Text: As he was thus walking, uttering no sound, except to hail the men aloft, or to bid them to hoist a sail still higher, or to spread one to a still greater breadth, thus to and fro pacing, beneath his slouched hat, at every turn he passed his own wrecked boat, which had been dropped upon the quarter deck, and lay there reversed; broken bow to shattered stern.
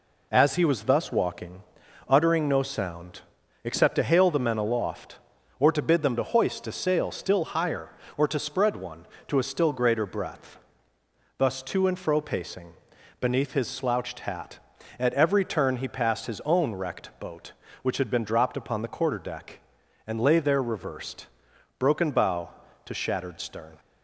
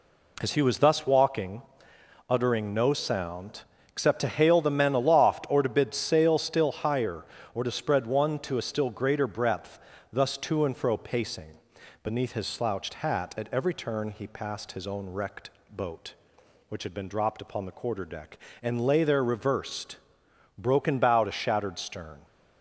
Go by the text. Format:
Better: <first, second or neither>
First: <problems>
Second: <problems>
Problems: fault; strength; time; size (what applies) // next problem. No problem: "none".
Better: first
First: none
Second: skips "them to hoist a"; at 5.9 s // pauses between "wrecked" and "boat"; slight; at 15.5 s; 0.20 s long